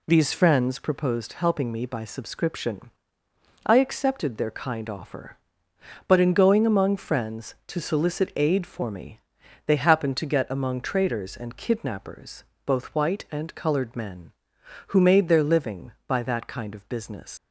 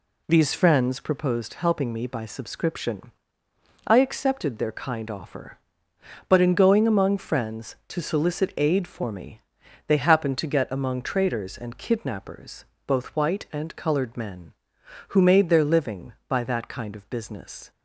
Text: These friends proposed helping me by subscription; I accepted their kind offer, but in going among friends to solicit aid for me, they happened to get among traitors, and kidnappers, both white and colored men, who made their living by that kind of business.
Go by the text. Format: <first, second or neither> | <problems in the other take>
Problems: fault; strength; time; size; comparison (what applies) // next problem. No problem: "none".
second | leaves "business" unfinished; at 17.3 s; 115 ms